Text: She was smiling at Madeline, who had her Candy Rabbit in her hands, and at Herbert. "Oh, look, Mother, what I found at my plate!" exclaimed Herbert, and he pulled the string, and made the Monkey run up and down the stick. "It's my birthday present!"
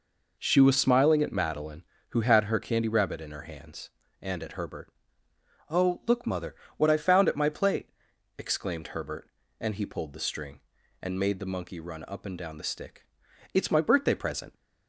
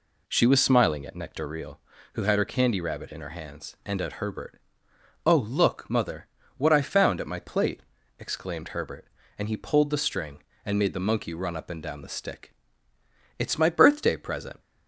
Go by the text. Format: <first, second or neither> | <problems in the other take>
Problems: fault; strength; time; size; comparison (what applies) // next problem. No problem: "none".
first | says "Nectareal" for "Madeline"; at 1.1 s